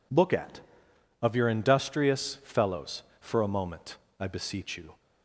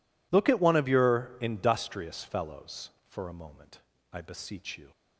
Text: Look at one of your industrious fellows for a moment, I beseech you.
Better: second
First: skips "one"; at 0.9 s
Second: none

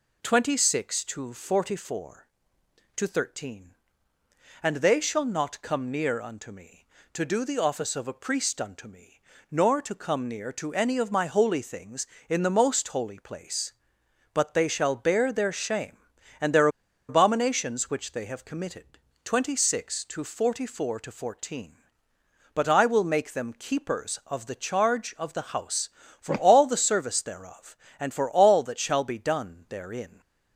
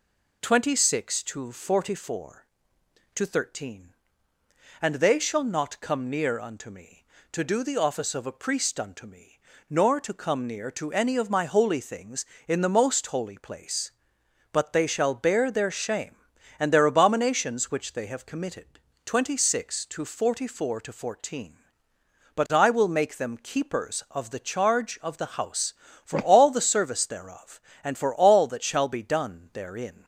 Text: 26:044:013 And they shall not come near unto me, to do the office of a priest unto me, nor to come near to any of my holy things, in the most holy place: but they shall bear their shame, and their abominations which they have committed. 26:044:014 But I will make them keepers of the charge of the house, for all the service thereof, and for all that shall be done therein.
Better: second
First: pauses between "their" and "abominations"; at 16.6 s; 0.40 s long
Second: none

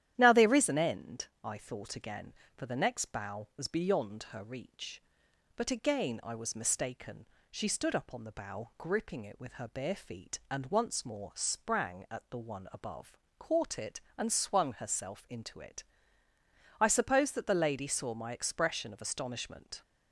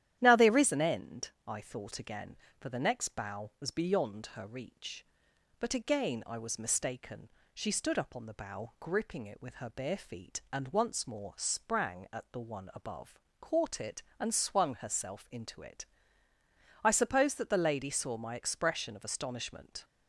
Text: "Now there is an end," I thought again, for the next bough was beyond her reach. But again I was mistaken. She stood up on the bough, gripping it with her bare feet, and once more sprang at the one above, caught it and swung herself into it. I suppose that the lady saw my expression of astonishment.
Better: neither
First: starts louder than the rest; strong; until 1.1 s; 11.5 dB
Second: starts louder than the rest; strong; until 1.2 s; 11.5 dB

